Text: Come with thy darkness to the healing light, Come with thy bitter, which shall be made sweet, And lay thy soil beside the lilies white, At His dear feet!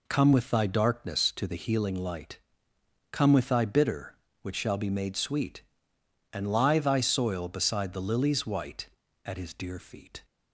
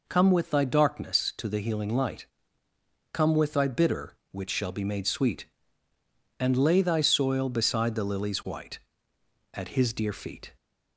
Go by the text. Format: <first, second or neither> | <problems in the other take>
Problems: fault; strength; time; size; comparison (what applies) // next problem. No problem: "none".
second | says "lie" for "lay"; at 6.5 s